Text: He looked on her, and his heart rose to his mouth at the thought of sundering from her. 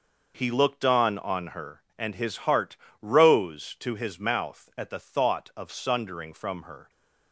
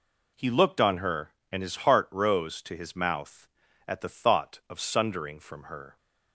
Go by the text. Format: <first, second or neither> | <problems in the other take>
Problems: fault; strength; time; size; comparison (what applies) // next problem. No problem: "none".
second | says "on" twice; at 1.1 s // pauses between "heart" and "rose"; slight; at 2.7 s; 0.24 s long